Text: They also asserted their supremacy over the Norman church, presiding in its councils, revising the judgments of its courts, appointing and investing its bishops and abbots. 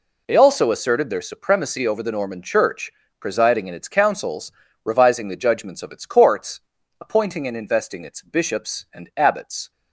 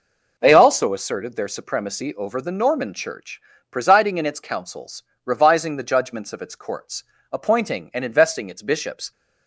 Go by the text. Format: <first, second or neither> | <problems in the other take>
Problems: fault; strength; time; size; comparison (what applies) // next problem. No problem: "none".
first | stops before "and abbots"; at 9.1 s